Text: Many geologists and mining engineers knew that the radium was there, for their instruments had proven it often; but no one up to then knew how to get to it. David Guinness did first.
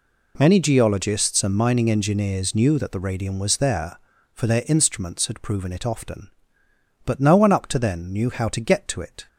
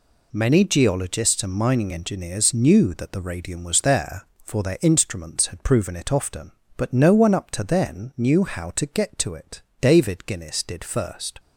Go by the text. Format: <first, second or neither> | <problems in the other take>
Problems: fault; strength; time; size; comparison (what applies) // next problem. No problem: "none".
second | stops before "David Guinness did first"; at 9.2 s